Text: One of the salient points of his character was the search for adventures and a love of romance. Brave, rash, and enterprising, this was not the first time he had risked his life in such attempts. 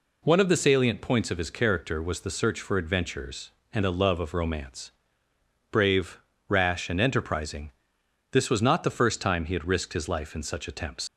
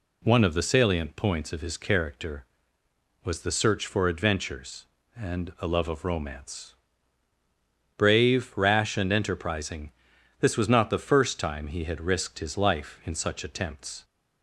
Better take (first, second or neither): second